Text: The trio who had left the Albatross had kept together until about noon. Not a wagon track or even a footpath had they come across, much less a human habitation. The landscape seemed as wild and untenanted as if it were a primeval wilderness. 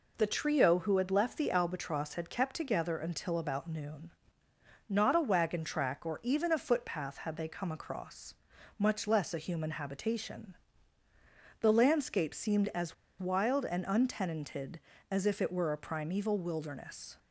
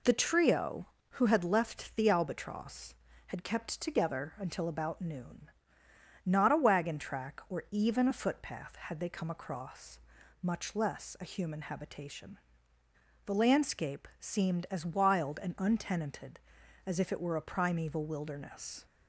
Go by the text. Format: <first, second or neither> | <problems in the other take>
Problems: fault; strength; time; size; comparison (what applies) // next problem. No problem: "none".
second | pauses between "as" and "wild"; slight; at 12.9 s; 0.24 s long